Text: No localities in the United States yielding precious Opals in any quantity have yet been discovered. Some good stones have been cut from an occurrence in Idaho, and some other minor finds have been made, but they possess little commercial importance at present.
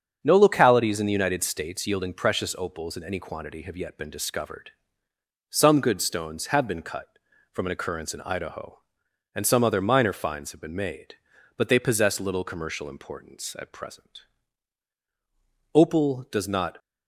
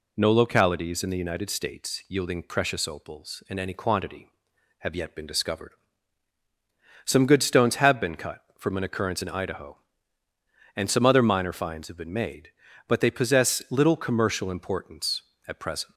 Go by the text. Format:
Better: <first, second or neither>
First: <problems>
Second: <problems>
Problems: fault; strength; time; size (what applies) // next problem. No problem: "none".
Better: second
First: starts louder than the rest; until 1.2 s; 7 dB // goes on to say "Opal does not"; noticeable; from 15.7 s on; 1.0 s long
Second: none